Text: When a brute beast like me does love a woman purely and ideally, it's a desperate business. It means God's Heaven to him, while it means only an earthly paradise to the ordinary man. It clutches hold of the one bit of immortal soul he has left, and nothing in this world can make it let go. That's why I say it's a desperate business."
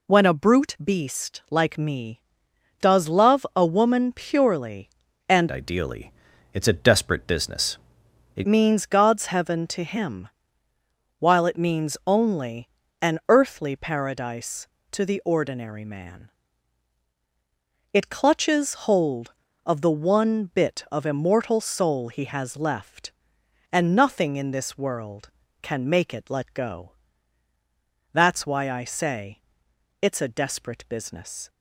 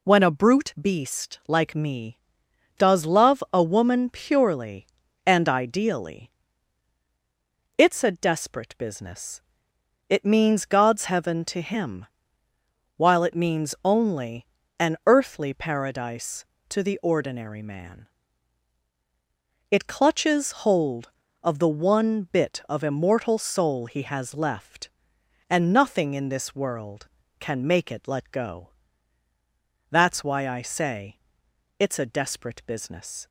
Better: second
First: changes voice from "ideally" to "It"; from 5.4 to 8.4 s; 3.0 s long // pauses between "only" and "an"; slight; at 12.6 s; 0.32 s long // pauses between "say" and "it's"; noticeable; at 29.3 s; 0.60 s long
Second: pauses between "only" and "an"; slight; at 14.4 s; 0.32 s long // pauses between "say" and "it's"; noticeable; at 31.1 s; 0.60 s long

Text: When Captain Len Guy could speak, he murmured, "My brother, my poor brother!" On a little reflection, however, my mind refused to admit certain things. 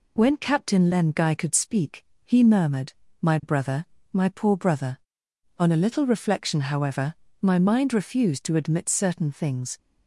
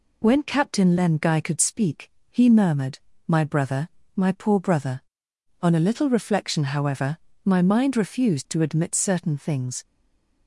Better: first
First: none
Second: stays silent after the last word; slight; from 9.8 s on; 0.6 s long

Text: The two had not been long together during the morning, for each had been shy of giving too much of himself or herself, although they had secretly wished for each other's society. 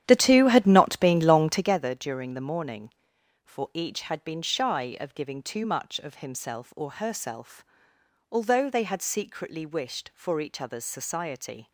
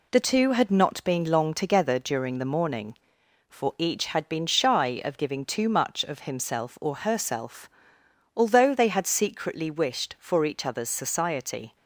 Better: second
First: starts louder than the rest; strong; until 1.8 s; 10.5 dB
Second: none

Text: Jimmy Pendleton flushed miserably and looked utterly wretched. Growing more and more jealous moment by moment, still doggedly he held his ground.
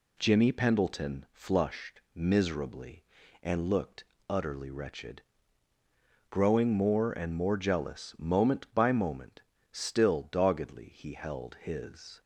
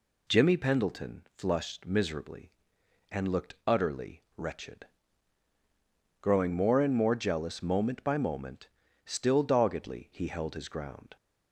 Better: second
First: pauses between "looked" and "utterly"; slight; at 4.0 s; 0.24 s long // stops before "ground"; at 12.1 s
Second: none

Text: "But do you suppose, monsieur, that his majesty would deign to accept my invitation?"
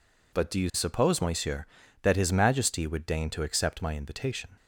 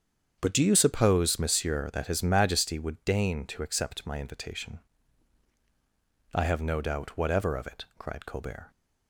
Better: first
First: none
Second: starts louder than the rest; strong; until 1.4 s; 8 dB // goes on to say "I have no doubt whatever of it cried Colbert"; strong; from 6.3 s on; 2.3 s long

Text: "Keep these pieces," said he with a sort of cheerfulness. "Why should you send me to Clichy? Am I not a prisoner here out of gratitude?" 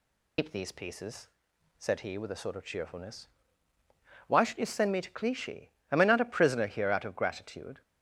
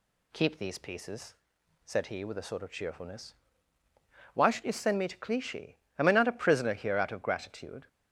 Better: second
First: loses the start of "Keep"; at 0.3 s; 125 ms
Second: none

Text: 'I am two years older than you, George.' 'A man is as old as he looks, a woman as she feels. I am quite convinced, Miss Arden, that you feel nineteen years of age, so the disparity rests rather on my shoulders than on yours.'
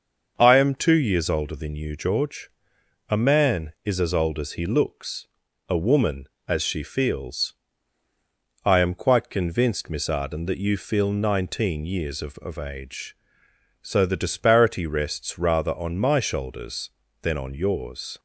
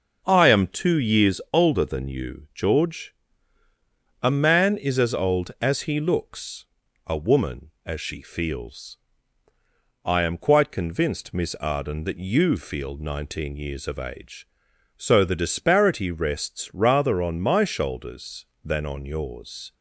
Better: second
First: starts louder than the rest; until 1.3 s; 6.5 dB // says "of" twice; at 12.3 s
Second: none

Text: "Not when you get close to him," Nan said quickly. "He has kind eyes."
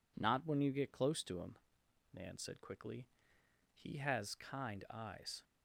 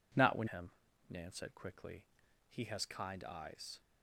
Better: first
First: none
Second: skips "you get close to"; at 0.4 s

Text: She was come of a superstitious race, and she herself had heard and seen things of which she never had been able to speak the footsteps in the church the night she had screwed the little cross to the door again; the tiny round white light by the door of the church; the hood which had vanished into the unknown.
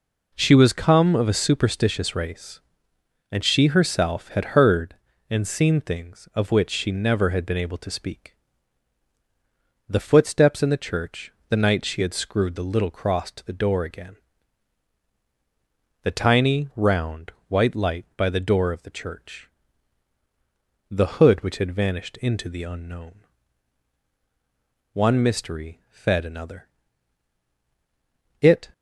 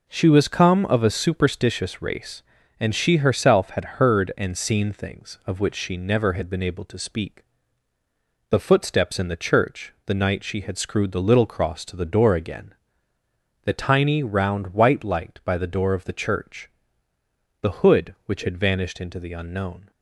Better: second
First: pauses between "speak" and "the"; strong; at 8.3 s; 1.5 s long // pauses between "church" and "the"; slight; at 11.3 s; 0.16 s long // pauses between "round" and "white"; slight; at 17.3 s; 0.18 s long // goes on to say "One mystery fed another It"; strong; from 24.9 s on; 3.7 s long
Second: pauses between "speak" and "the"; at 7.4 s; 1.0 s long

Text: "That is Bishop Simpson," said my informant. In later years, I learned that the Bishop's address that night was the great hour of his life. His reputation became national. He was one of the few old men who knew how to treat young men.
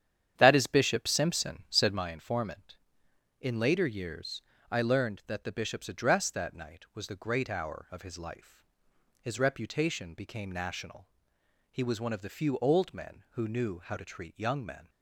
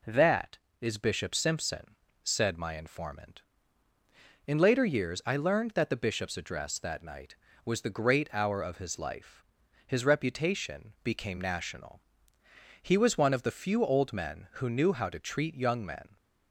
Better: second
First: starts louder than the rest; strong; until 2.1 s; 9.5 dB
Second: none

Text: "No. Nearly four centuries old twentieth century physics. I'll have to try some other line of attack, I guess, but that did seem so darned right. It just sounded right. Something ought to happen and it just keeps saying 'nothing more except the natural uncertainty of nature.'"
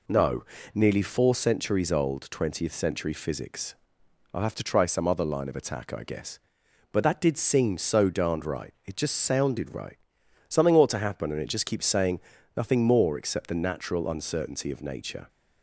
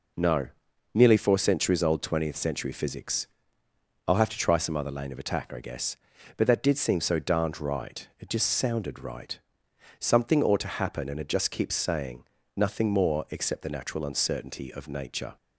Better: first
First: pauses between "saying" and "nothing"; slight; at 12.1 s; 0.36 s long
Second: says "lane" for "line"; at 4.9 s // pauses between "saying" and "nothing"; slight; at 12.2 s; 0.32 s long

